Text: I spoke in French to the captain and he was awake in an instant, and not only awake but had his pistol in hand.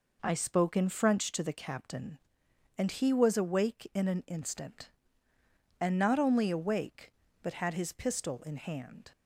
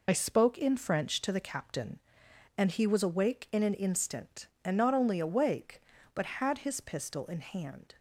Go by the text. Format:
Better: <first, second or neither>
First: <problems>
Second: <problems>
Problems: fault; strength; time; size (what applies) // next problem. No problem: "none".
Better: first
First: none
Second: loses the start of "I"; at 0.0 s; 50 ms